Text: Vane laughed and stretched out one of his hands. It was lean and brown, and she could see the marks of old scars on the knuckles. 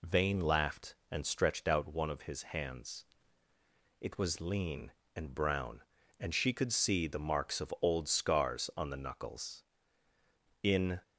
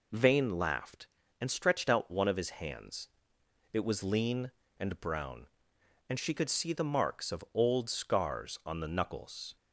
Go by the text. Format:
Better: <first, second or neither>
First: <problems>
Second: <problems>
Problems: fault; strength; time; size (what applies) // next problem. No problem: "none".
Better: second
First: goes on to say "In"; slight; from 10.6 s on; 0.38 s long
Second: none